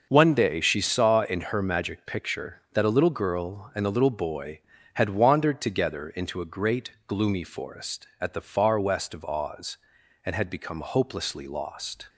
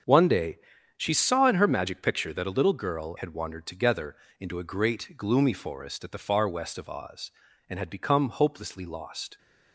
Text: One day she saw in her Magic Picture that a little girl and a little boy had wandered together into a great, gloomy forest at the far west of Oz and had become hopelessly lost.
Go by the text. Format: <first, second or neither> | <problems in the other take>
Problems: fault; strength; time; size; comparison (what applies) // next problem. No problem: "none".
first | starts louder than the rest; strong; until 1.4 s; 7.5 dB; noticeable in the first // pauses between "day" and "she"; at 0.5 s; 0.40 s long // skips "and a little boy"; at 3.1 s // pauses between "together" and "into"; slight; at 4.1 s; 0.24 s long